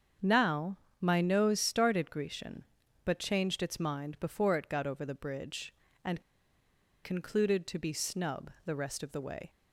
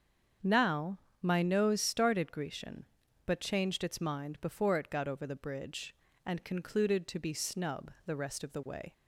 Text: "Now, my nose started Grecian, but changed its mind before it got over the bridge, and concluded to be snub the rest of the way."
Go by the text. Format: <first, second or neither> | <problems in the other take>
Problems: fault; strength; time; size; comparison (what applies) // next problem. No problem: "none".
second | starts louder than the rest; strong; until 1.4 s; 7.5 dB; strong in the second // pauses between "and" and "concluded"; noticeable; at 6.2 s; 0.82 s long // pauses between "snub" and "the"; slight; at 8.4 s; 0.16 s long; slight in the second